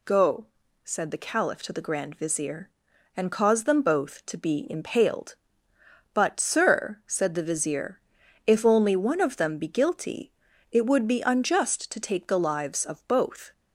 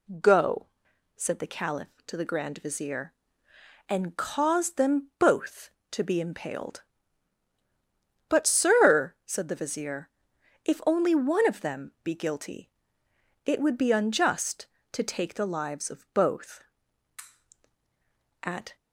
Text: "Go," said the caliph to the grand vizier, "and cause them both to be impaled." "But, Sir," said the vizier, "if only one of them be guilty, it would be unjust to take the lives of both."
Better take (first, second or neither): first